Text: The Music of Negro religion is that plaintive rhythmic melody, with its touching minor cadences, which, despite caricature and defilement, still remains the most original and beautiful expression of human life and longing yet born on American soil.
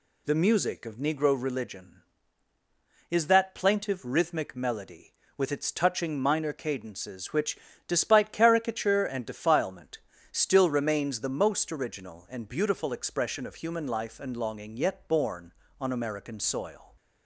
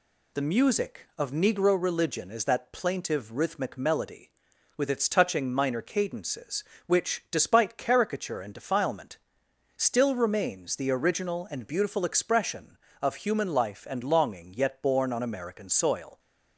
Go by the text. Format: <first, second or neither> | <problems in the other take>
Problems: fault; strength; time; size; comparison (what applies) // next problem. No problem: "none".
first | skips "most"; at 10.8 s